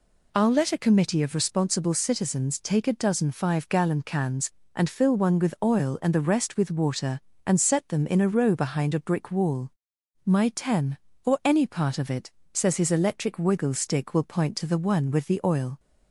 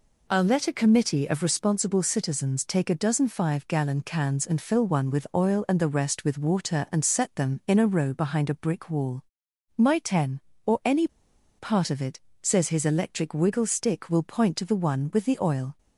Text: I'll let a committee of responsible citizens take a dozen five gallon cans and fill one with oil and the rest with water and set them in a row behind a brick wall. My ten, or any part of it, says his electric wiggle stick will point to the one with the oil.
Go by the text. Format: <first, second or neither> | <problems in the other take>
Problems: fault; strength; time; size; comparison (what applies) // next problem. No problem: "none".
first | pauses between "any" and "part"; noticeable; at 11.0 s; 0.50 s long